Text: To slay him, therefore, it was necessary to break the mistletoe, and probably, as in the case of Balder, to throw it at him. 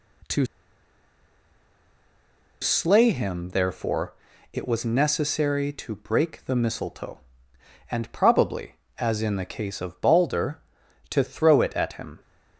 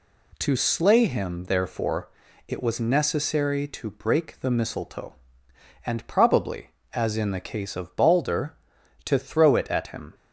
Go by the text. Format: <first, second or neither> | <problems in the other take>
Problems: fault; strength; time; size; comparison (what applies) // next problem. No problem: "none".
second | pauses between "To" and "slay"; strong; at 0.4 s; 2.1 s long